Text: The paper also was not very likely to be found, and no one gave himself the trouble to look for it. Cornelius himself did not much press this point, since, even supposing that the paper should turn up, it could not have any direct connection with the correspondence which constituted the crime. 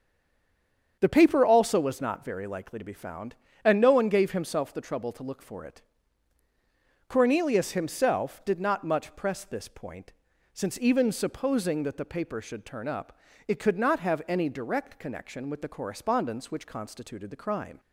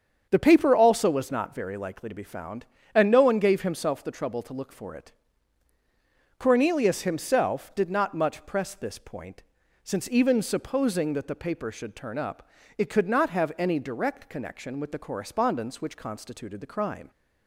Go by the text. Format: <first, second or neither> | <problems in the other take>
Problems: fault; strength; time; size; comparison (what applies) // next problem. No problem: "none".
second | stays silent before the first word; until 0.9 s; 0.9 s long // starts louder than the rest; strong; until 2.0 s; 7.5 dB; strong in the second